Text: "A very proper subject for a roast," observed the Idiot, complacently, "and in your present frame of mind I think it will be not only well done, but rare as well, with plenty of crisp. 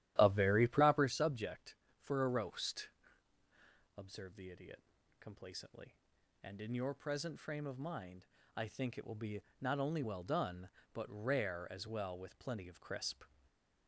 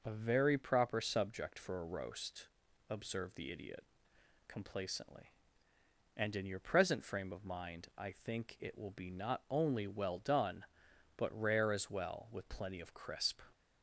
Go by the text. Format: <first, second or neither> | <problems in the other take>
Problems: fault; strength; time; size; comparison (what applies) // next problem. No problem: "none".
second | starts louder than the rest; strong; until 1.2 s; 13 dB // pauses between "mind" and "I"; slight; at 8.2 s; 0.30 s long // pauses between "be" and "not"; slight; at 9.4 s; 0.18 s long // stays silent after the last word; slight; from 13.2 s on; 0.6 s long